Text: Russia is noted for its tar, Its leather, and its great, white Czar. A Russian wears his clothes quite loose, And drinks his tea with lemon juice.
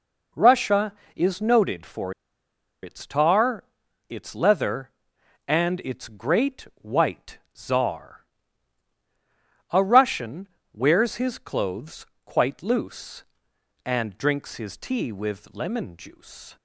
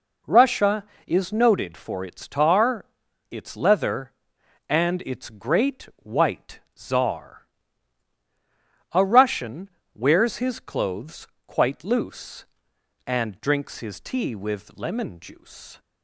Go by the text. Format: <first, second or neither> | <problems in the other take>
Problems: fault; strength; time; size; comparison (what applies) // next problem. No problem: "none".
second | pauses between "for" and "its"; noticeable; at 2.1 s; 0.70 s long // pauses between "white" and "Czar"; slight; at 7.3 s; 0.18 s long; slight in the second // pauses between "Russian" and "wears"; slight; at 10.4 s; 0.26 s long; slight in the second // pauses between "clothes" and "quite"; slight; at 12.0 s; 0.18 s long; slight in the second